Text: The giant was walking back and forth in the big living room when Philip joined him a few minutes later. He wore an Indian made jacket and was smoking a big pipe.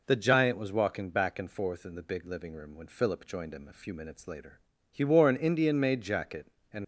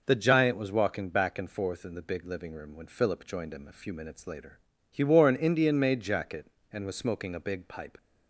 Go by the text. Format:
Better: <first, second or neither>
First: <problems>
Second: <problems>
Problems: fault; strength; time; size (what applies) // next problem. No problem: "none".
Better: second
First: stops before "was smoking a big pipe"; at 6.8 s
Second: none